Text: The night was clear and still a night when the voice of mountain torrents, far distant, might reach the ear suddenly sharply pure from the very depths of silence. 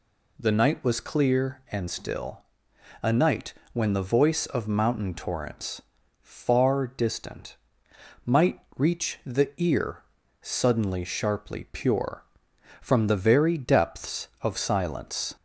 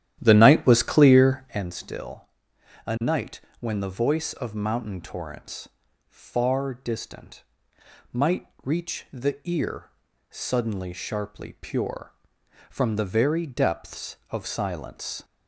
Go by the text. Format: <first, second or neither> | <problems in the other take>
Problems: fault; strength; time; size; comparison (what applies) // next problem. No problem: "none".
first | starts louder than the rest; strong; until 1.7 s; 11.5 dB // pauses between "still" and "a"; noticeable; at 2.2 s; 0.60 s long; noticeable in the first // pauses between "night" and "when"; slight; at 3.3 s; 0.20 s long; slight in the first // pauses between "might" and "reach"; slight; at 8.4 s; 0.16 s long; slight in the first // pauses between "ear" and "suddenly"; at 9.8 s; 0.42 s long; also in the first